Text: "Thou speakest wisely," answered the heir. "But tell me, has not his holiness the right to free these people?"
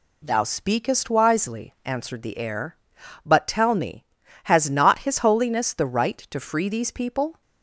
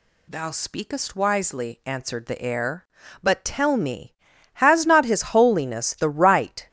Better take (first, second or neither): first